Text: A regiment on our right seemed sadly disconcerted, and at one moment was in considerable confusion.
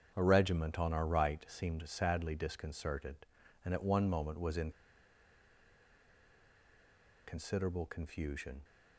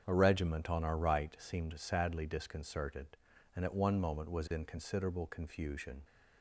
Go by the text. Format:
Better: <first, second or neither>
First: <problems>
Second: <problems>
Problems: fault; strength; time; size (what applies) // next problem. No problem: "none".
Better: second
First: starts louder than the rest; strong; until 1.1 s; 7.5 dB // pauses between "in" and "considerable"; strong; at 4.7 s; 2.5 s long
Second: starts louder than the rest; strong; until 1.0 s; 7.5 dB